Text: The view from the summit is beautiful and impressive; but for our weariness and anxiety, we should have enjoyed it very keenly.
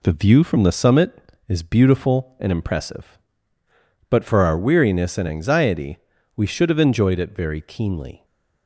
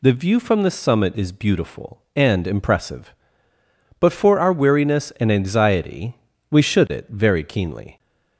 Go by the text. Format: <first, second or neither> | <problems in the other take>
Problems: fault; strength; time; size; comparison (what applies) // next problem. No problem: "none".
first | skips "have enjoyed"; at 6.8 s